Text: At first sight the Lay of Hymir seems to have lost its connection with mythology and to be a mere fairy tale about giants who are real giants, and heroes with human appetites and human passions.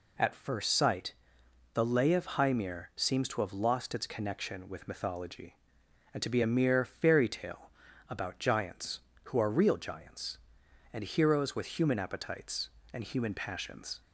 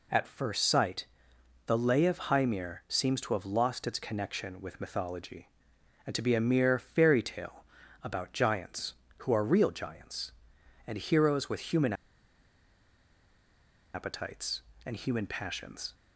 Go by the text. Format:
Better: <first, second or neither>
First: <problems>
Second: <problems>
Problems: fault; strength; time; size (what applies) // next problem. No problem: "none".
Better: first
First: pauses between "sight" and "the"; noticeable; at 1.1 s; 0.62 s long // pauses between "tale" and "about"; at 7.6 s; 0.38 s long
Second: pauses between "sight" and "the"; noticeable; at 1.0 s; 0.62 s long // pauses between "tale" and "about"; at 7.6 s; 0.38 s long // pauses between "human" and "appetites"; strong; at 11.9 s; 2.0 s long